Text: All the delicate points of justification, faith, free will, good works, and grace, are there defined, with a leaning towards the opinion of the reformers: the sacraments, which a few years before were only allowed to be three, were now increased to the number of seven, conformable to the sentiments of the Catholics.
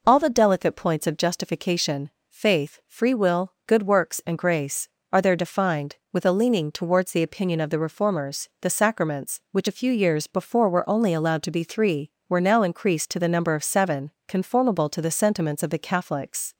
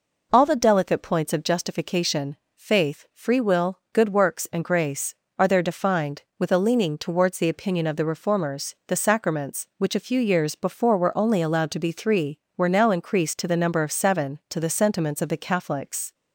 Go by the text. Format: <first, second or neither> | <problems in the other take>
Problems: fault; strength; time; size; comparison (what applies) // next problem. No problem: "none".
first | skips "conformable"; at 14.4 s